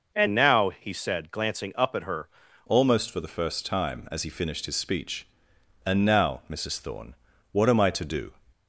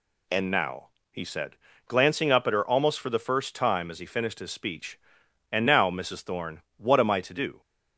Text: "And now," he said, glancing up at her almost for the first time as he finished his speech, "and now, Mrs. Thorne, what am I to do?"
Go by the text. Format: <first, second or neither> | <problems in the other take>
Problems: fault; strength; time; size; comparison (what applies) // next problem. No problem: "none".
second | changes voice at "almost"; from 2.6 s on; 5.7 s long